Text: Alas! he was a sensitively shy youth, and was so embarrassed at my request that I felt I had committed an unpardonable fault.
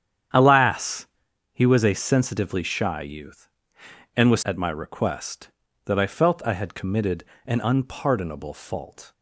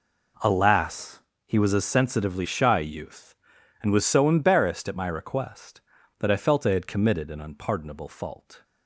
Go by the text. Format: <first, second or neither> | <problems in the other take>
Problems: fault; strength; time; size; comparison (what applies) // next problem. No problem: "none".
second | starts louder than the rest; strong; until 1.7 s; 9 dB // skips "so embarrassed"; at 4.4 s // pauses between "committed" and "an"; slight; at 7.2 s; 0.20 s long